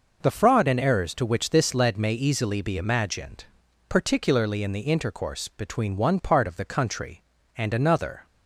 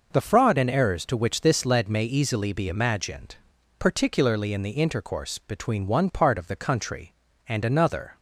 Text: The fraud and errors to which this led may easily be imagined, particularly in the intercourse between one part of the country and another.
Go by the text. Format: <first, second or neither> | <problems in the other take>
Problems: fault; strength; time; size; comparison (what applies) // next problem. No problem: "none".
neither | none